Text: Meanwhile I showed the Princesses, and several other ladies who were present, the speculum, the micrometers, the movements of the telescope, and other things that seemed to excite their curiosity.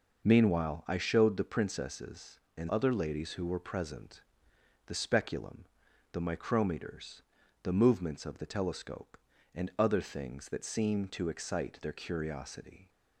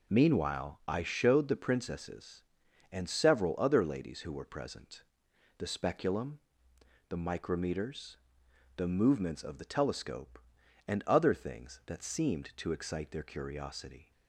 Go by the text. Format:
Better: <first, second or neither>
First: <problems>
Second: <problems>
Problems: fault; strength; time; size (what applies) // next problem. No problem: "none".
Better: second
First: skips "several"; at 2.6 s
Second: none